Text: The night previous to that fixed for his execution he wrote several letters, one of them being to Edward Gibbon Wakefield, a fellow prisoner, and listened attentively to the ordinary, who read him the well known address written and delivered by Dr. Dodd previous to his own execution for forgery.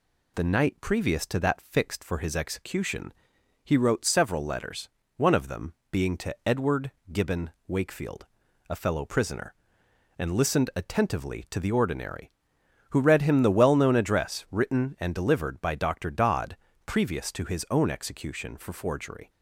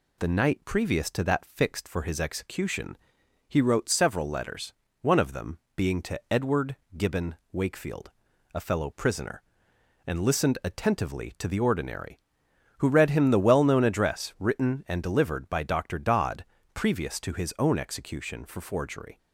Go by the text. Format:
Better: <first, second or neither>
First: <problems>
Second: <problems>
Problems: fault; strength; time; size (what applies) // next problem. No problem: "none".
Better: neither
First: pauses between "execution" and "he"; noticeable; at 3.1 s; 0.54 s long // pauses between "them" and "being"; slight; at 5.7 s; 0.18 s long // pauses between "Edward" and "Gibbon"; slight; at 6.9 s; 0.20 s long // pauses between "Gibbon" and "Wakefield"; slight; at 7.5 s; 0.16 s long // pauses between "Dodd" and "previous"; slight; at 16.5 s; 0.32 s long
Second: pauses between "execution" and "he"; noticeable; at 2.9 s; 0.54 s long // pauses between "them" and "being"; slight; at 5.5 s; 0.18 s long // pauses between "Edward" and "Gibbon"; slight; at 6.7 s; 0.20 s long // pauses between "Gibbon" and "Wakefield"; slight; at 7.3 s; 0.16 s long // pauses between "Dodd" and "previous"; slight; at 16.4 s; 0.32 s long